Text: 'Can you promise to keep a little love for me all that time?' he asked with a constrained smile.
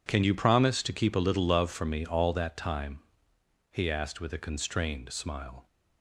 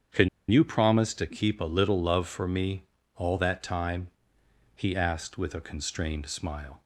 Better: first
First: none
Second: starts louder than the rest; strong; until 1.3 s; 8 dB // pauses between "Can" and "you"; slight; at 0.2 s; 0.22 s long // pauses between "me" and "all"; slight; at 2.8 s; 0.32 s long

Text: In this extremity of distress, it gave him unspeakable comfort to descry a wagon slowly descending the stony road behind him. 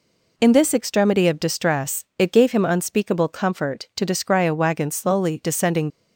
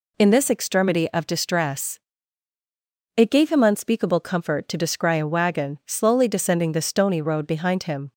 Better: second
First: stops before "the stony road behind him"; at 5.9 s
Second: none

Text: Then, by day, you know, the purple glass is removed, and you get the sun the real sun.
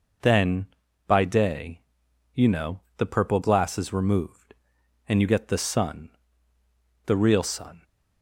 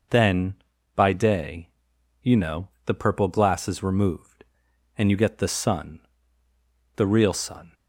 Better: neither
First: pauses between "sun" and "the"; noticeable; at 6.0 s; 0.96 s long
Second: pauses between "sun" and "the"; noticeable; at 5.9 s; 0.96 s long

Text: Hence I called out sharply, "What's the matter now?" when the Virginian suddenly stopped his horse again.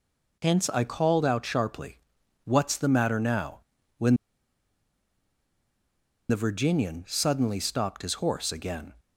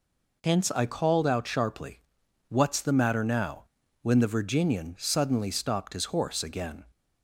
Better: second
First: pauses between "when" and "the"; strong; at 4.1 s; 2.1 s long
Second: none

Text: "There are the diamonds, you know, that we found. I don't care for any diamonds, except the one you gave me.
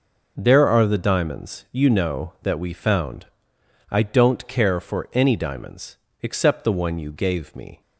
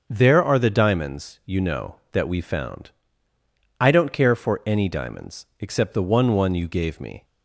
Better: first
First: none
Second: starts louder than the rest; until 1.1 s; 6 dB // says "one" twice; at 6.3 s

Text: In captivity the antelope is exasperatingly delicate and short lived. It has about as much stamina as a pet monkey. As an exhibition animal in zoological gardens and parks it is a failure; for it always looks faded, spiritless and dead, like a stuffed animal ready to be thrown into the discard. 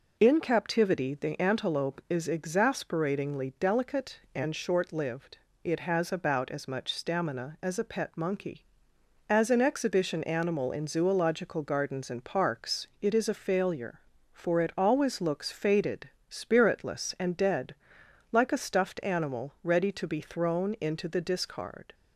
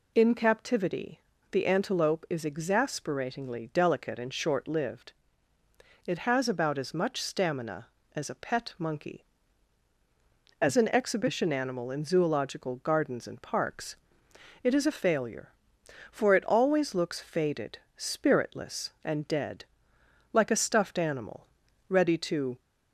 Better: first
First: none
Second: pauses between "captivity" and "the"; slight; at 1.2 s; 0.30 s long // pauses between "parks" and "it"; noticeable; at 13.9 s; 0.66 s long // pauses between "animal" and "ready"; at 21.4 s; 0.42 s long // stops before "be thrown into the discard"; at 22.5 s

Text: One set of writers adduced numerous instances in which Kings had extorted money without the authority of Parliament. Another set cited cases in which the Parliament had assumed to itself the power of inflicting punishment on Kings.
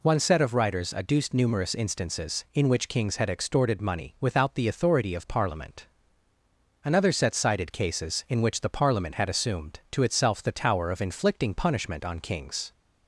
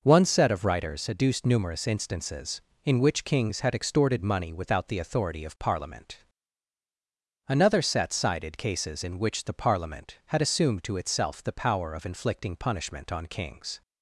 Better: second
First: says "tower" for "power"; at 10.4 s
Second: none

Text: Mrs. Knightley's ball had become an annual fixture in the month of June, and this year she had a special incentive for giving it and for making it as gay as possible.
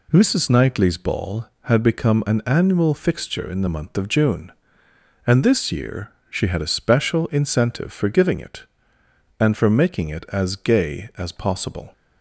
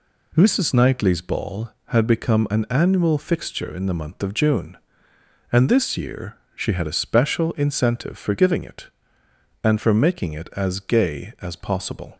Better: neither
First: pauses between "year" and "she"; slight; at 6.1 s; 0.18 s long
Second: pauses between "year" and "she"; slight; at 6.3 s; 0.18 s long

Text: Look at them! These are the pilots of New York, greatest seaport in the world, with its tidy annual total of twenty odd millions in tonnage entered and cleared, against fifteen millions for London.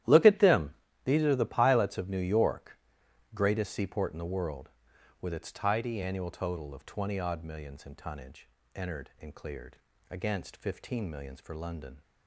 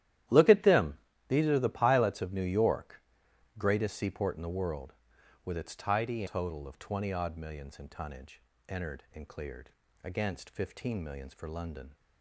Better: first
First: starts louder than the rest; strong; until 1.3 s; 12.5 dB // pauses between "tonnage" and "entered"; slight; at 8.4 s; 0.26 s long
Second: starts louder than the rest; strong; until 1.6 s; 12 dB // skips "annual"; at 6.2 s // pauses between "tonnage" and "entered"; slight; at 8.4 s; 0.26 s long

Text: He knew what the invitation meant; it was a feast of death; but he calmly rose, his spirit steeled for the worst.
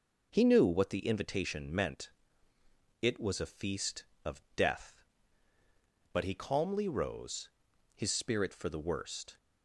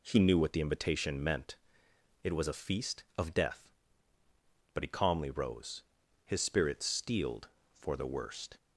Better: second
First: skips "steeled"; at 8.5 s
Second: none

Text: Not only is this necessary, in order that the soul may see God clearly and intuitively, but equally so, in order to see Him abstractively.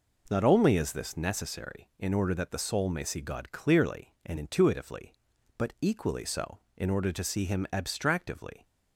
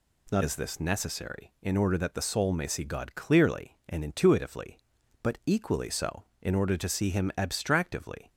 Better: first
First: none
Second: skips "only"; at 0.4 s

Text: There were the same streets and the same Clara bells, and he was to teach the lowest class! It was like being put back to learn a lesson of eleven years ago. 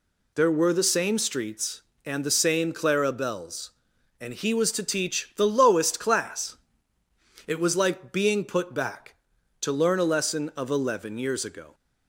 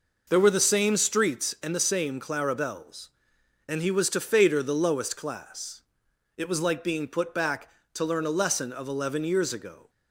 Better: first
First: none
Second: says "fader" for "teach"; at 4.2 s

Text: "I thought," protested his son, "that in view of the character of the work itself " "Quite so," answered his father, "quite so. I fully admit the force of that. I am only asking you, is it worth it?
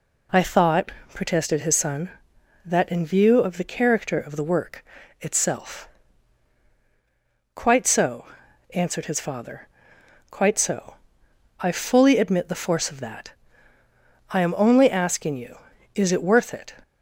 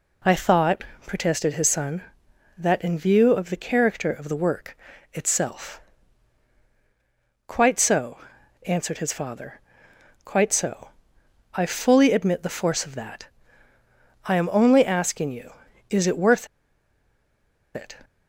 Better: first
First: pauses between "work" and "itself"; slight; at 4.8 s; 0.36 s long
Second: pauses between "work" and "itself"; slight; at 4.7 s; 0.36 s long // pauses between "worth" and "it"; strong; at 16.4 s; 1.2 s long

